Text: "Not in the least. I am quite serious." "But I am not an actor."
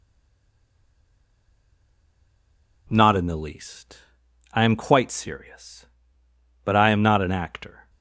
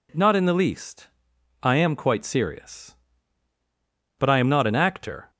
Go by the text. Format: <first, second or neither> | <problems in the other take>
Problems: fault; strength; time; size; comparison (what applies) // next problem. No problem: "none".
second | stays silent before the first word; strong; until 2.8 s; 2.8 s long